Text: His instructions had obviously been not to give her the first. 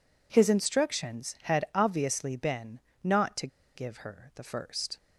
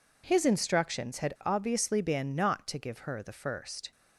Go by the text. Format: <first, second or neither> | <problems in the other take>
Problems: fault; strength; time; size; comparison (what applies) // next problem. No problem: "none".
second | pauses between "been" and "not"; slight; at 2.7 s; 0.24 s long // pauses between "to" and "give"; slight; at 3.4 s; 0.28 s long